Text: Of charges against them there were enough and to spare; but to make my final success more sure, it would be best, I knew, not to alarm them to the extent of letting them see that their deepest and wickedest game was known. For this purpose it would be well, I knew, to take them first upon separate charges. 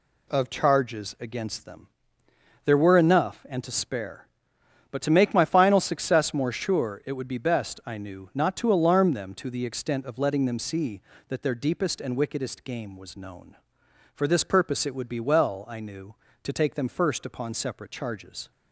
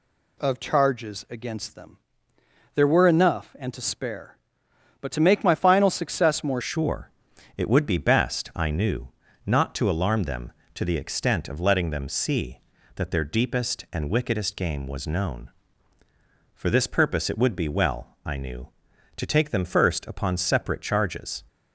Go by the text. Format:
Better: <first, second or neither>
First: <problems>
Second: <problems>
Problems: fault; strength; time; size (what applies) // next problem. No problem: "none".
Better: first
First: pauses between "them" and "there"; noticeable; at 1.8 s; 0.78 s long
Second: pauses between "them" and "there"; noticeable; at 1.9 s; 0.78 s long // changes voice at "sure"; from 6.5 s on; 14.9 s long